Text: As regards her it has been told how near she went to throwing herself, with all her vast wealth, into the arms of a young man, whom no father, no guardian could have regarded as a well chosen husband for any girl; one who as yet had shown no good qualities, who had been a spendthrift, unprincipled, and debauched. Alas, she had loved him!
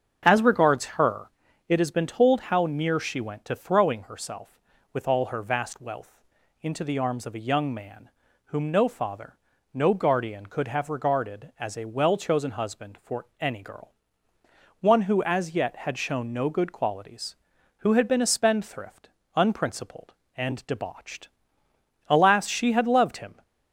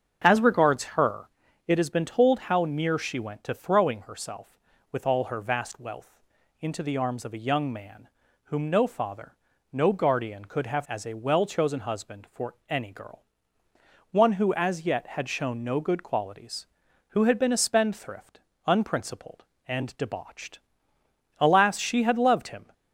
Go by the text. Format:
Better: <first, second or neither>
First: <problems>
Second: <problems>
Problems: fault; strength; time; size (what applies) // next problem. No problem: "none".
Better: first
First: starts louder than the rest; strong; until 1.2 s; 7 dB // pauses between "her" and "it"; at 1.2 s; 0.38 s long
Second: starts louder than the rest; strong; until 1.2 s; 7 dB // pauses between "her" and "it"; at 1.2 s; 0.38 s long // skips "regarded"; at 10.8 s